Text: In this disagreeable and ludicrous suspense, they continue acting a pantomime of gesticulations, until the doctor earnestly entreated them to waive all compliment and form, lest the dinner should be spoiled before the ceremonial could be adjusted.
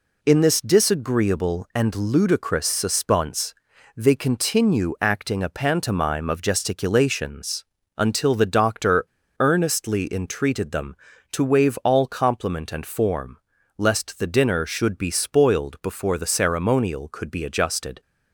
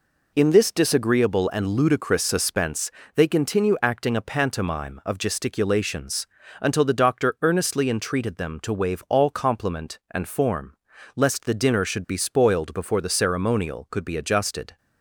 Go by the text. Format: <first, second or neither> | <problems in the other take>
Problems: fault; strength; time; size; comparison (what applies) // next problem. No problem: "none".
second | pauses between "doctor" and "earnestly"; slight; at 9.0 s; 0.32 s long